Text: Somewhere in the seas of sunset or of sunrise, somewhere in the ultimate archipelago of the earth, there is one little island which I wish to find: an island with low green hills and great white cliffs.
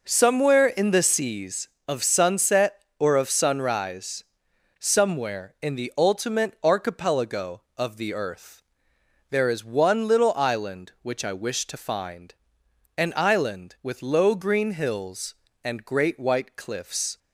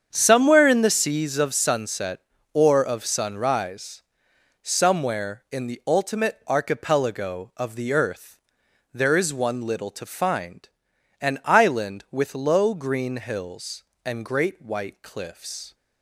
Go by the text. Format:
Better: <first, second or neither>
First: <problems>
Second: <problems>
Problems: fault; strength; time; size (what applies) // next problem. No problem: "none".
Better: first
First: none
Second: starts louder than the rest; strong; until 1.1 s; 7.5 dB // skips "island which I wish"; at 9.9 s